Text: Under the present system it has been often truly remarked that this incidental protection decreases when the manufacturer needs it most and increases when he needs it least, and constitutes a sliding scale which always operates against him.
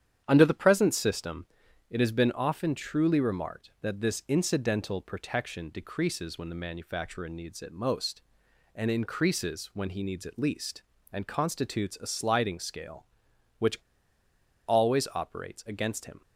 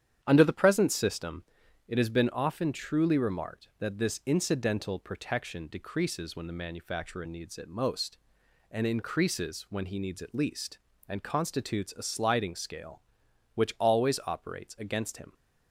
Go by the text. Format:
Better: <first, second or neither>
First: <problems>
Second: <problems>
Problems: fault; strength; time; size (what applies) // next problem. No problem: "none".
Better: second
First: starts louder than the rest; strong; until 1.2 s; 9.5 dB // pauses between "system" and "it"; at 1.4 s; 0.44 s long // pauses between "which" and "always"; noticeable; at 13.7 s; 0.90 s long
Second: starts louder than the rest; strong; until 1.2 s; 9.5 dB // pauses between "system" and "it"; at 1.4 s; 0.44 s long